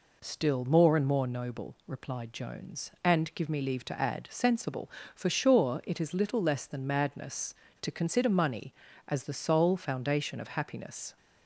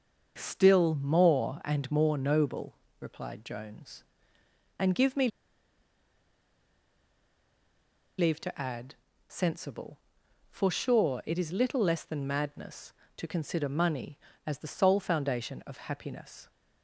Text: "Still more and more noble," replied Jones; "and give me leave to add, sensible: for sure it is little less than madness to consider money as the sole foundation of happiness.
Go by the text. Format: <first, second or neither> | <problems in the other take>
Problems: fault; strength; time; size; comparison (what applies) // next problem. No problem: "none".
first | starts louder than the rest; until 1.3 s; 6.5 dB // pauses between "me" and "leave"; strong; at 5.2 s; 2.8 s long